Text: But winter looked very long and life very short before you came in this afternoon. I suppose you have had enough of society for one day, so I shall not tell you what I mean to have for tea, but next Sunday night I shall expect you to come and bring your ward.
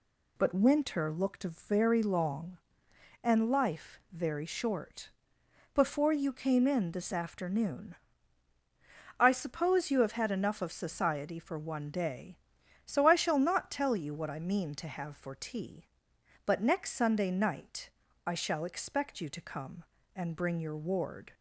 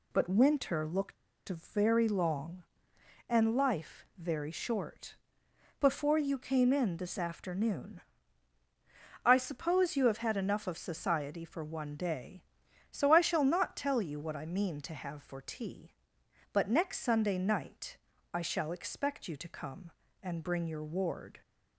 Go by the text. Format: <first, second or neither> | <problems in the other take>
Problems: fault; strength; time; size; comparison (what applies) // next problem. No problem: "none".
first | pauses between "looked" and "very"; slight; at 1.1 s; 0.33 s long // pauses between "short" and "before"; noticeable; at 5.1 s; 0.64 s long; noticeable in the first // pauses between "night" and "I"; slight; at 17.9 s; 0.36 s long; slight in the first